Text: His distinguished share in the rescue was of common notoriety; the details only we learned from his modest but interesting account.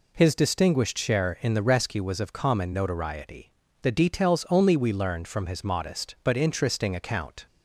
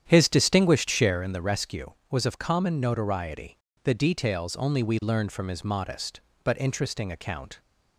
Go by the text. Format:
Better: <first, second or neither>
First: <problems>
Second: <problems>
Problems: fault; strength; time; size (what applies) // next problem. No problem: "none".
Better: first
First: none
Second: starts louder than the rest; strong; until 1.4 s; 9.5 dB